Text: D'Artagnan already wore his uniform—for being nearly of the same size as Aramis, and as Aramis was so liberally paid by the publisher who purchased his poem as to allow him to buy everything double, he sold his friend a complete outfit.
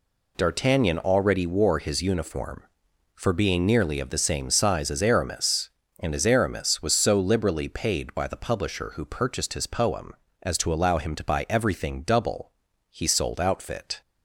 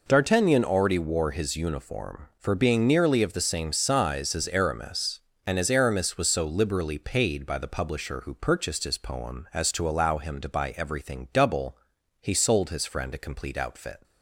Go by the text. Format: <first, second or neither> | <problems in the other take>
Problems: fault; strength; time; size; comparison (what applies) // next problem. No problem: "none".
second | skips "his friend a complete"; at 13.3 s